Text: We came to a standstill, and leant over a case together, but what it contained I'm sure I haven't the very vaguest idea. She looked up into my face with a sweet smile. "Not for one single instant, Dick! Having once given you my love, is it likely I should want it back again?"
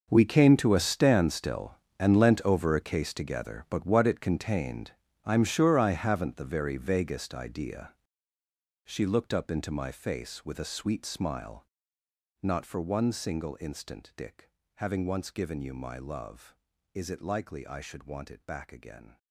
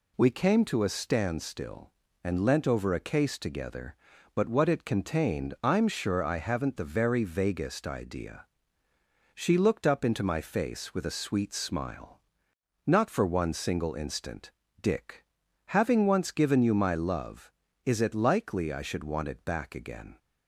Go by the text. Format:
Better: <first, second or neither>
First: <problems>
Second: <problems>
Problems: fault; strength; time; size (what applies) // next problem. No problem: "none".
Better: second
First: gets quieter; strong; throughout; 16.5 dB // pauses between "contained" and "I'm"; slight; at 4.9 s; 0.34 s long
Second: none